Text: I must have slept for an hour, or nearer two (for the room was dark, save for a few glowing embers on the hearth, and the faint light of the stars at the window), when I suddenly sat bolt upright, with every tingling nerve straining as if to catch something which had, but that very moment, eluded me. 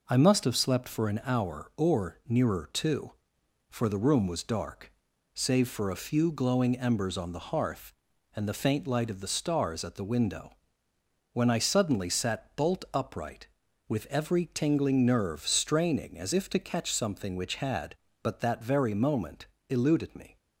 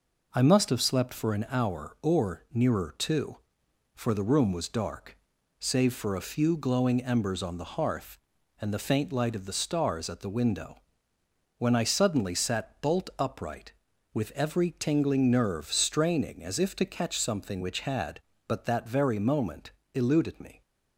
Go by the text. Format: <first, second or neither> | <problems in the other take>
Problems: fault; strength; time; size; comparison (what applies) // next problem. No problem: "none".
neither | none